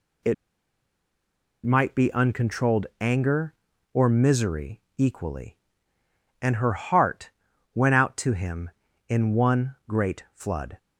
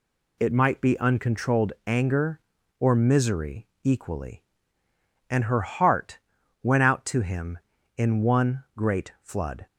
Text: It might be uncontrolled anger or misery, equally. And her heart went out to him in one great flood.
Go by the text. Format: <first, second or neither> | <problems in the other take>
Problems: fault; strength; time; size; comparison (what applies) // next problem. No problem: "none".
second | pauses between "It" and "might"; strong; at 0.3 s; 1.3 s long // pauses between "heart" and "went"; at 7.2 s; 0.44 s long; also in the second